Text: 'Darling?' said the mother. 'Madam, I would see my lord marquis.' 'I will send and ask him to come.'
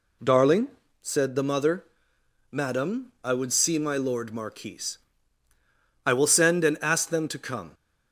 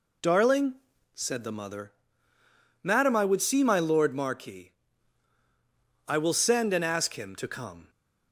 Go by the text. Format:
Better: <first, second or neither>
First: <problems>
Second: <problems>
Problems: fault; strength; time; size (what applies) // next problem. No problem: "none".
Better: second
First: says "them" for "him"; at 7.0 s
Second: none